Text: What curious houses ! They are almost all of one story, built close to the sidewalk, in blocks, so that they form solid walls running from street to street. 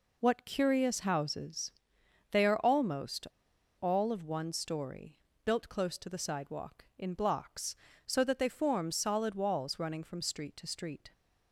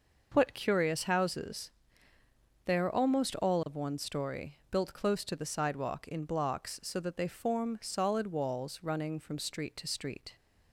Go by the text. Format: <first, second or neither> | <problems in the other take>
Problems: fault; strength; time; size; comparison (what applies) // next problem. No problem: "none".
second | pauses between "almost" and "all"; noticeable; at 3.2 s; 0.54 s long